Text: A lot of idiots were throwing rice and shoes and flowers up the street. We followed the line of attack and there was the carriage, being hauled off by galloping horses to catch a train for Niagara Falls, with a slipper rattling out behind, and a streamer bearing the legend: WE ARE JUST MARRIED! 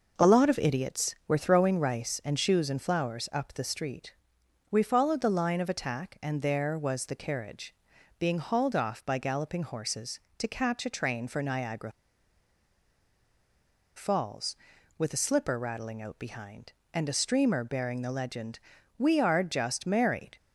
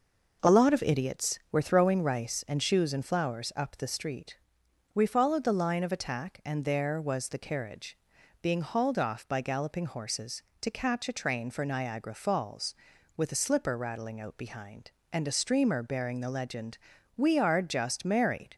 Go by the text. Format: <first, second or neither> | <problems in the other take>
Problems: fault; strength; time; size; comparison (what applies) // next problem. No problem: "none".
second | pauses between "Niagara" and "Falls"; strong; at 11.9 s; 2.0 s long